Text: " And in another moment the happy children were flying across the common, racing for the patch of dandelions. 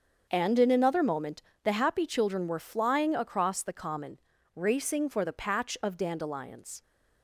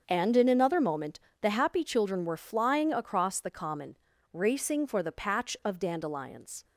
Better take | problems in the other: neither | starts louder than the rest; the same in both // pauses between "moment" and "the"; slight; the same in both

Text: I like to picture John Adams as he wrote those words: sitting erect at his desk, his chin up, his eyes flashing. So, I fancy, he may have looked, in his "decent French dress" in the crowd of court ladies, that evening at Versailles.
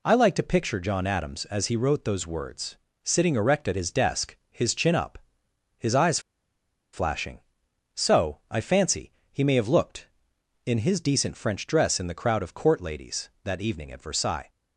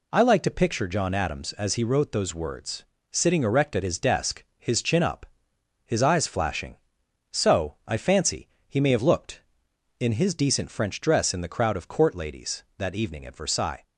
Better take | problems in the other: second | pauses between "eyes" and "flashing"; noticeable; at 6.1 s; 0.73 s long

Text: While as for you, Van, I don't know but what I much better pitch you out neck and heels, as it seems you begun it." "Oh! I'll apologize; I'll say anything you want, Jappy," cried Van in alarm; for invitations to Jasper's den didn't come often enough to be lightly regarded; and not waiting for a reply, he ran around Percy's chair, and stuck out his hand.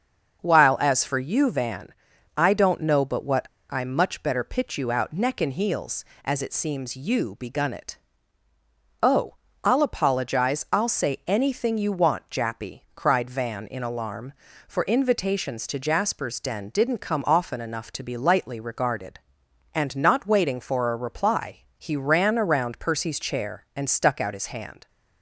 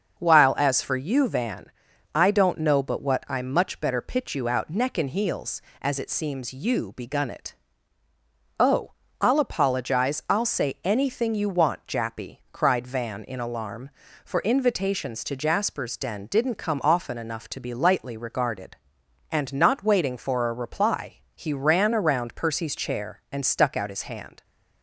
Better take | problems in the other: second | starts louder than the rest; until 1.4 s; 7 dB; also in the second // pauses between "what" and "I"; slight; at 3.4 s; 0.21 s long

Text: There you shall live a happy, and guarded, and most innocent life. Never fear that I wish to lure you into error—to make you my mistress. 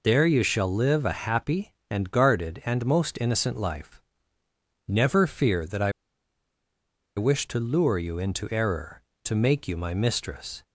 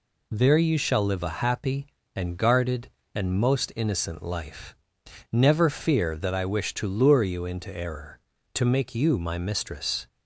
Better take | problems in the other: second | pauses between "I" and "wish"; strong; at 5.9 s; 1.2 s long

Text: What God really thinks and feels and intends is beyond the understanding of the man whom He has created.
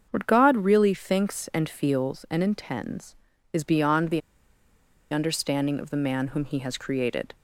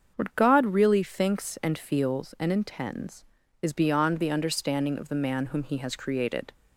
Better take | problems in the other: second | starts louder than the rest; until 1.1 s; 7 dB; also in the second // pauses between "the" and "understanding"; noticeable; at 4.2 s; 0.92 s long

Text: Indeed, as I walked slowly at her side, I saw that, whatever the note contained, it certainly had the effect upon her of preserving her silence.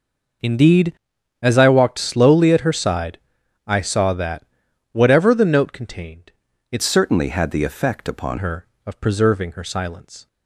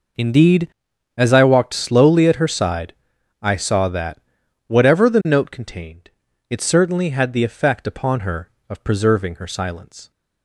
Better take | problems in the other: second | changes voice from "certainly" to "upon"; from 6.8 to 8.3 s; 1.5 s long

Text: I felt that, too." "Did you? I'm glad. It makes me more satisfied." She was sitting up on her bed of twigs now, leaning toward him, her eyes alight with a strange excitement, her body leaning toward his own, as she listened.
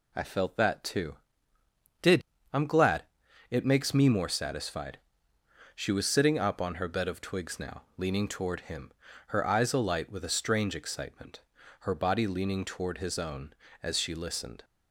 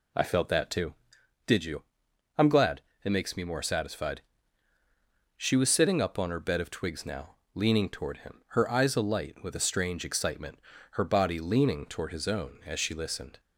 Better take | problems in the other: second | skips "you"; at 2.3 s

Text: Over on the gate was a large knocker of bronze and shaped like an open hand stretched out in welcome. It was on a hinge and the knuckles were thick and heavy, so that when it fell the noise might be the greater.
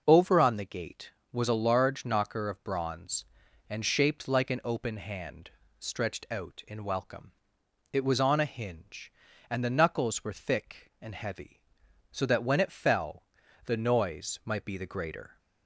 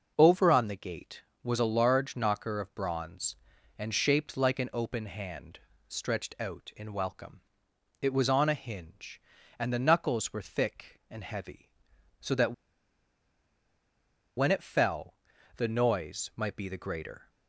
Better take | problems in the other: first | pauses between "hand" and "stretched"; slight; at 5.5 s; 0.30 s long; slight in the first // pauses between "that" and "when"; strong; at 12.5 s; 1.8 s long // pauses between "fell" and "the"; at 15.1 s; 0.40 s long; also in the first

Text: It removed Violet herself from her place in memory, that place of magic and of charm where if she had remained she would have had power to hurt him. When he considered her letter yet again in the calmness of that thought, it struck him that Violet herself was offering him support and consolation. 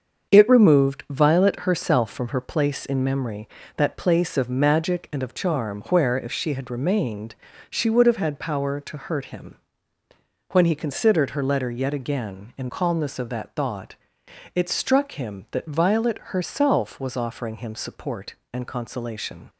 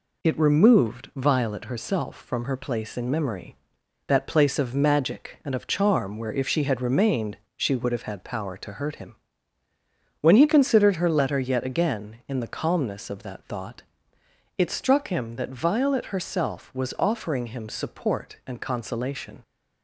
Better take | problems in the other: second | starts louder than the rest; until 1.3 s; 7 dB // pauses between "remained" and "she"; slight; at 7.3 s; 0.36 s long; slight in the second // skips "the"; at 12.6 s

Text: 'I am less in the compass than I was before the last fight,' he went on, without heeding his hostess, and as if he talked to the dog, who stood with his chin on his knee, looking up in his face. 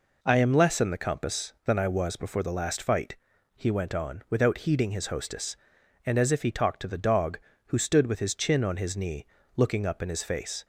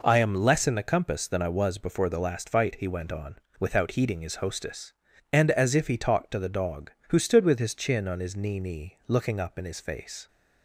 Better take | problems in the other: first | says "knee" twice; at 8.5 s

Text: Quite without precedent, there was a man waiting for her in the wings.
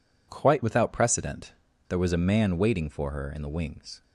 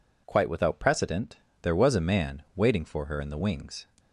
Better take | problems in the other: neither | none

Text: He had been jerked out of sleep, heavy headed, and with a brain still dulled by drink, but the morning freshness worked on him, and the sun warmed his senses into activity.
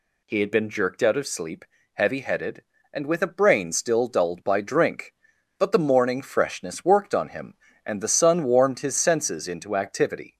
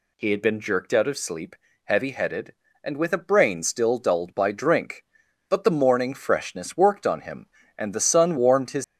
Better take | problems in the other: first | stops before "senses into activity"; at 8.8 s

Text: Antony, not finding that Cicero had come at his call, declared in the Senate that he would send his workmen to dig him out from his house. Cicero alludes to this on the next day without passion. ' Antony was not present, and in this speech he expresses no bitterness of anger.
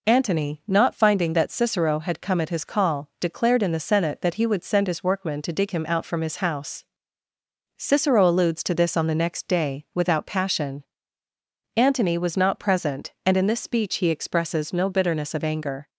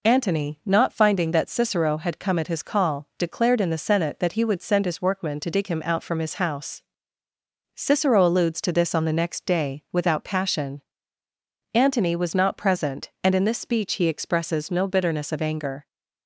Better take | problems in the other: neither | none

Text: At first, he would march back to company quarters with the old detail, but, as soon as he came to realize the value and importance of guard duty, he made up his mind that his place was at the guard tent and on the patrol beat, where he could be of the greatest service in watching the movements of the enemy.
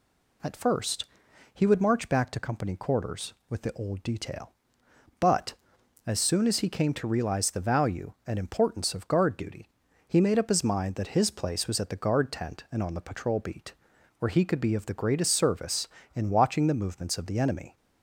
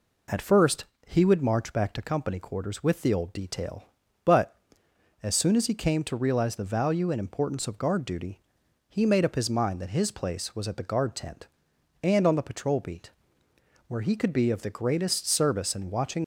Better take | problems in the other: first | stops before "the movements of the enemy"; at 16.2 s

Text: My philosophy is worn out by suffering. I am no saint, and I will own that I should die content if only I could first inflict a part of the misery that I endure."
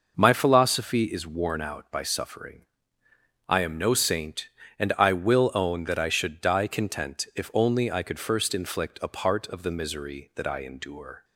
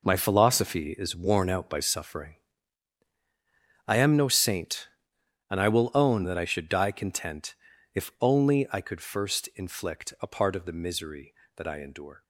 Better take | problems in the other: first | gets quieter; strong; throughout; 12 dB // pauses between "content" and "if"; at 7.5 s; 0.38 s long

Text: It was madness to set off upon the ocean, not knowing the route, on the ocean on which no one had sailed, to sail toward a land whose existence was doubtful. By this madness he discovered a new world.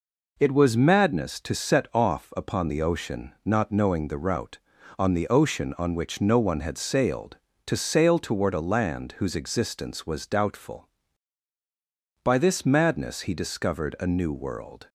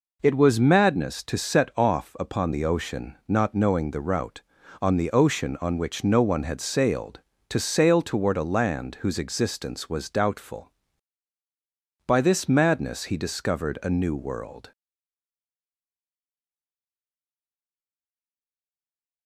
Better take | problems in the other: first | stays silent after the last word; strong; from 14.7 s on; 4.5 s long

